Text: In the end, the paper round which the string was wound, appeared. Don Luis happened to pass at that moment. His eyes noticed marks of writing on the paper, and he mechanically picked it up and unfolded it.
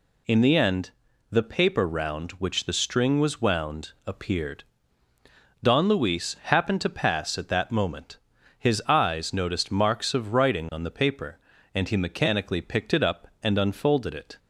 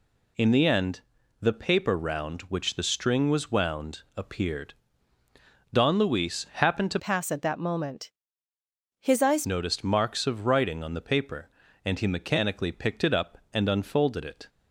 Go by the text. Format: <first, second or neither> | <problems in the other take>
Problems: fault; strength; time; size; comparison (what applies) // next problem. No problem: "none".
first | changes voice from "pass" to "eyes"; from 6.9 to 9.4 s; 2.5 s long